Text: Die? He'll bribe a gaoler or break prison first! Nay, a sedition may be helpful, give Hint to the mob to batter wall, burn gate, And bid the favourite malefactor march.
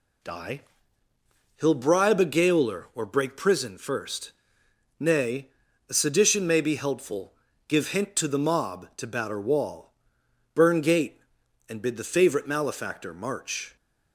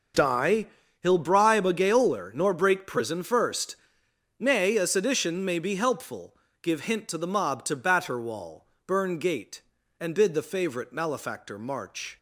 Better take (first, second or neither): first